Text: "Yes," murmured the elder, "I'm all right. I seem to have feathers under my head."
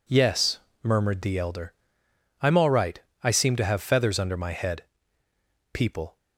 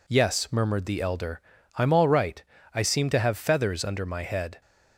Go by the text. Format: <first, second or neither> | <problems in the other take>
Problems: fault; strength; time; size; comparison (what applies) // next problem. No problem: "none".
second | goes on to say "People"; slight; from 5.7 s on; 0.44 s long